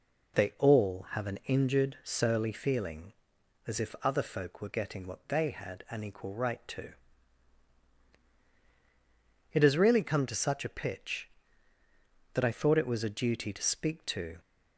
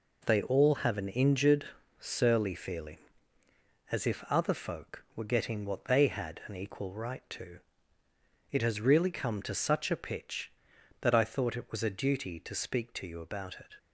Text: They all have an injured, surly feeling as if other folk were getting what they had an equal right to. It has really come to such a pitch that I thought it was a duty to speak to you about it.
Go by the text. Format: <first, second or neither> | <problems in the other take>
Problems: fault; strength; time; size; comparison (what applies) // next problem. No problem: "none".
second | stops before "you about it"; at 14.3 s